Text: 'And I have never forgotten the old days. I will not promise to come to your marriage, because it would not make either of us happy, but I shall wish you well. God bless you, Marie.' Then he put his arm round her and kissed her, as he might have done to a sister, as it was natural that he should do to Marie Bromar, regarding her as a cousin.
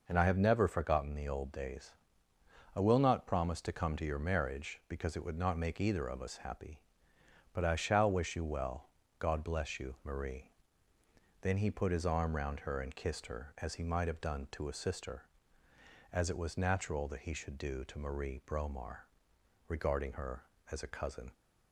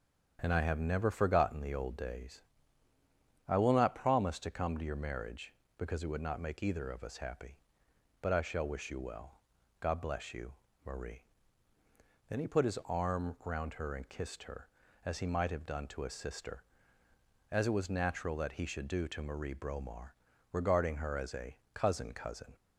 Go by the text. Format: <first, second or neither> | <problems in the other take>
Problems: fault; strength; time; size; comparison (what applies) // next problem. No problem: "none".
first | starts louder than the rest; strong; until 1.4 s; 8 dB // pauses between "a" and "cousin"; slight; at 21.5 s; 0.18 s long // says "cousin" twice; at 22.1 s